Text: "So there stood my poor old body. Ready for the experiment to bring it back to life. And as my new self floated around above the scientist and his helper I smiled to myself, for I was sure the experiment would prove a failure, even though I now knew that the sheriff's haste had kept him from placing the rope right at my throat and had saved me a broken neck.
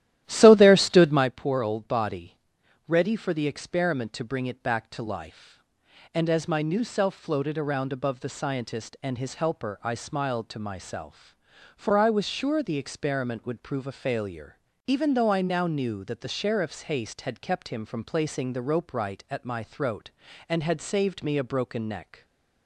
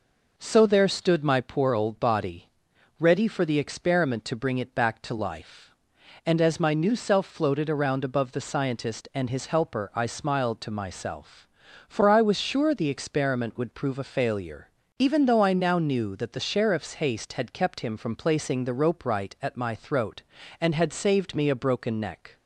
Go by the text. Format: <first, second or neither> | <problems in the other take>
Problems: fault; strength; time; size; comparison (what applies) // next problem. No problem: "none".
second | starts louder than the rest; strong; until 1.3 s; 13 dB // stays silent after the last word; slight; from 22.1 s on; 0.5 s long